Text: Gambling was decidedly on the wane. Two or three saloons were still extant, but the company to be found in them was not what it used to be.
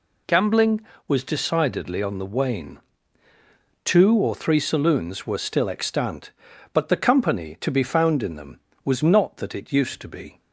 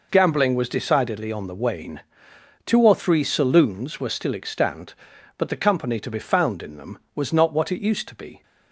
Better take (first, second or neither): second